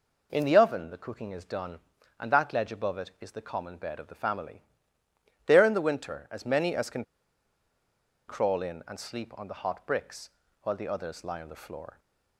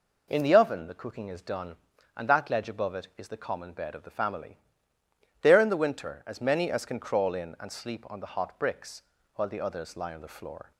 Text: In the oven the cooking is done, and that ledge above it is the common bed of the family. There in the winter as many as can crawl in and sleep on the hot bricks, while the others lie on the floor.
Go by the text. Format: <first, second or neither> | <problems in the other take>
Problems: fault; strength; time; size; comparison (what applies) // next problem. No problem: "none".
second | pauses between "can" and "crawl"; at 7.0 s; 1.2 s long